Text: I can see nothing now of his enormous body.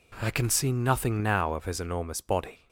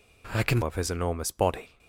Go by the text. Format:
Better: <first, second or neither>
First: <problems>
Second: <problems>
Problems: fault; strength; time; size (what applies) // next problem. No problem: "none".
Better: first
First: none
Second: skips "see nothing now"; at 0.6 s